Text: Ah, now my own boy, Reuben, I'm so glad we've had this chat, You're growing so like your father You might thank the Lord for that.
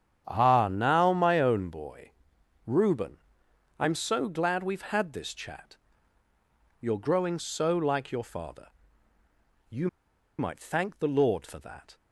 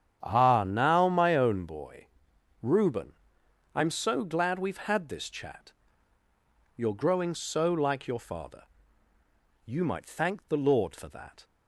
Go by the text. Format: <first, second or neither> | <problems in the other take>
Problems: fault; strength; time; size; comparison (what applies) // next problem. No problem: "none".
second | starts louder than the rest; strong; until 1.2 s; 9 dB; strong in the second // pauses between "father" and "You"; at 8.6 s; 1.0 s long; also in the second // pauses between "You" and "might"; noticeable; at 9.8 s; 0.51 s long